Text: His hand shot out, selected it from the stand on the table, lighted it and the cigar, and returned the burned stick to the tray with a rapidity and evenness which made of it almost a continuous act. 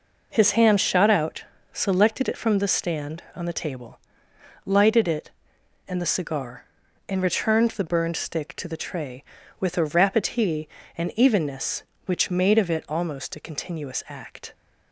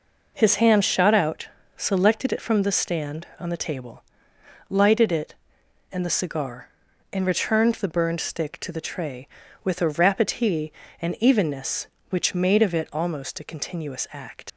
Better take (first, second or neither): first